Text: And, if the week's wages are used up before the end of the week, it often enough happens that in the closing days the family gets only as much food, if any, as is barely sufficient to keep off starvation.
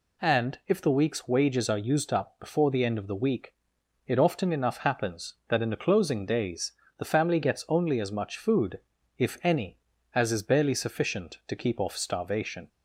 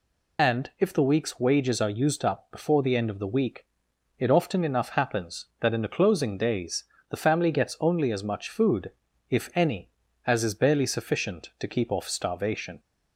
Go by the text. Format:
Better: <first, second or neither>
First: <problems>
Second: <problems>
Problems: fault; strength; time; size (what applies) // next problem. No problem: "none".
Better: first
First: pauses between "days" and "the"; slight; at 6.7 s; 0.26 s long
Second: loses the start of "And"; at 0.3 s; 65 ms // pauses between "days" and "the"; slight; at 6.8 s; 0.26 s long